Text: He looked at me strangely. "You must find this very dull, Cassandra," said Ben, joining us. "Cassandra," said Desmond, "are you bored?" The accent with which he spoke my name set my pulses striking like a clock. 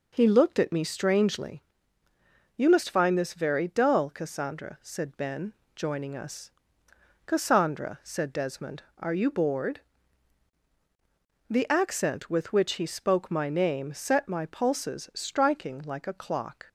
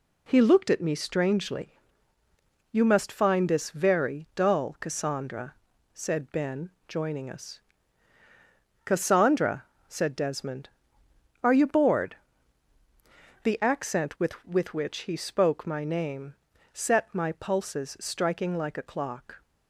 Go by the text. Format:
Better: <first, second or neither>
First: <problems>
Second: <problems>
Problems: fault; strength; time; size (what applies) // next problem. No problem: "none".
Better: first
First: none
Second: says "with" twice; at 14.4 s // pauses between "name" and "set"; at 16.3 s; 0.38 s long